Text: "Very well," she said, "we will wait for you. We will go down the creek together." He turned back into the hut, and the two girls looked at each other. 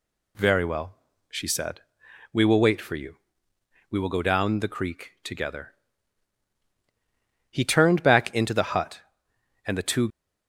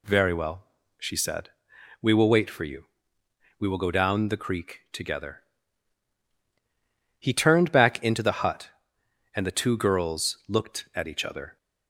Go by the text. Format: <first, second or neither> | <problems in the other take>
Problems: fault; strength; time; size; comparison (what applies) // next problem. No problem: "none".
second | stops before "girls looked at each other"; at 10.0 s